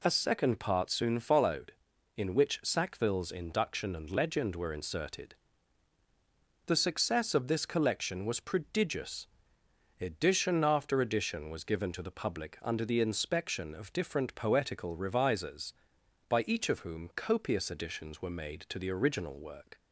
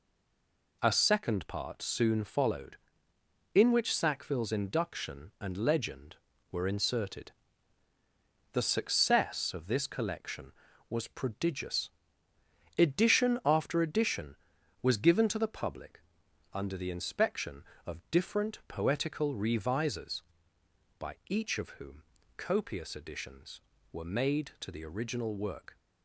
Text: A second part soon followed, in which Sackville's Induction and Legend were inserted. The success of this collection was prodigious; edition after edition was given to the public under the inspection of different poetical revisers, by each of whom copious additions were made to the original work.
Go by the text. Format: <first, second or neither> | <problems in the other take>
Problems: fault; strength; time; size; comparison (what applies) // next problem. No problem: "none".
first | stays silent before the first word; slight; until 0.8 s; 0.8 s long // pauses between "public" and "under"; noticeable; at 16.0 s; 0.52 s long // pauses between "whom" and "copious"; slight; at 22.0 s; 0.34 s long